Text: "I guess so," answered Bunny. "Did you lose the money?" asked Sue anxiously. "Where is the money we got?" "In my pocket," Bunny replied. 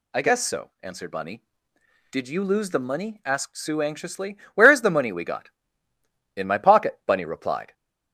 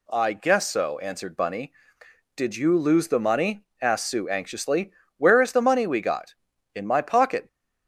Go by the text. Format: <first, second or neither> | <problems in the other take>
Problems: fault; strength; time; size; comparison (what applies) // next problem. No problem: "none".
first | stops before "Bunny replied"; at 7.4 s